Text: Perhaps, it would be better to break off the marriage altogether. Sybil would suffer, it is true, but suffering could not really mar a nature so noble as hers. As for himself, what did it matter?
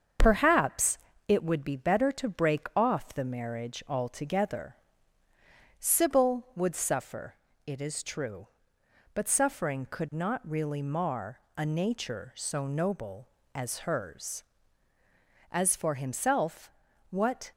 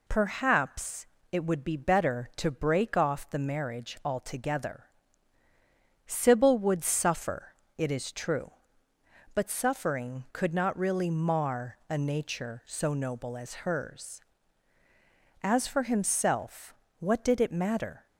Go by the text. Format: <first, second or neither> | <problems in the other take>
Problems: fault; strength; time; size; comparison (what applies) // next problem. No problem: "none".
second | starts louder than the rest; until 1.4 s; 7 dB // pauses between "mar" and "a"; slight; at 11.3 s; 0.18 s long // stops before "did it matter"; at 17.5 s